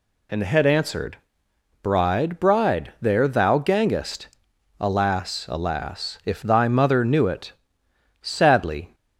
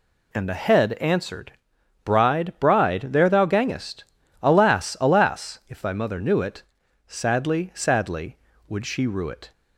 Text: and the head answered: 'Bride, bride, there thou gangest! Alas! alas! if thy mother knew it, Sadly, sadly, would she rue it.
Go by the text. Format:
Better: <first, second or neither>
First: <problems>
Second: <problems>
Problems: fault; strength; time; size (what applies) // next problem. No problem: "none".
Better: second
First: stops before "sadly would she rue it"; at 8.9 s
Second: none